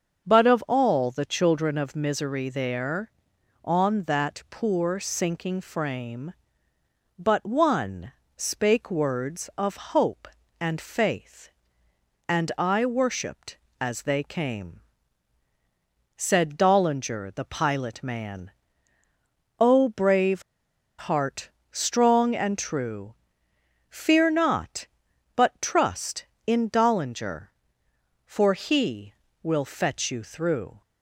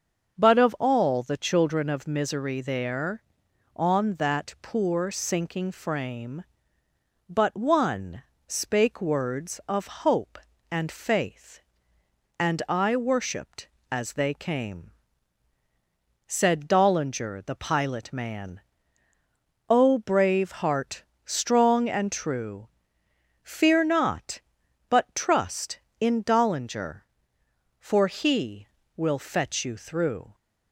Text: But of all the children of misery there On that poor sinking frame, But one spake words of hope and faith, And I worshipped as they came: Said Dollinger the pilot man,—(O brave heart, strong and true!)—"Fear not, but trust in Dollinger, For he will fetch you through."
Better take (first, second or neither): second